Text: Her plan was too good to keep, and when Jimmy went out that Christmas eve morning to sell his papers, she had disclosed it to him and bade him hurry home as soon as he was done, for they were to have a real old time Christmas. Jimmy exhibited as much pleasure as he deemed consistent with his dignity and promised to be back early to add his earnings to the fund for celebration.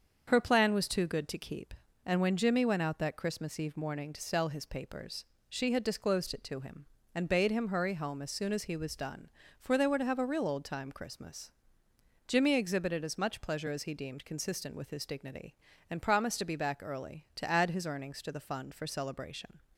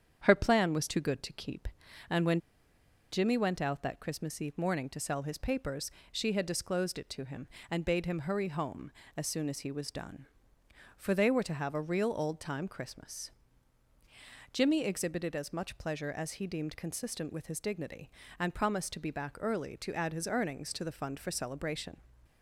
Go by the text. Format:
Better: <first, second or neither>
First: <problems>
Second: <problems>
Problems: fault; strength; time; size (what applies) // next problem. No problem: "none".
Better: first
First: starts louder than the rest; until 1.3 s; 7 dB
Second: starts louder than the rest; strong; until 1.2 s; 8 dB // pauses between "when" and "Jimmy"; noticeable; at 2.4 s; 0.71 s long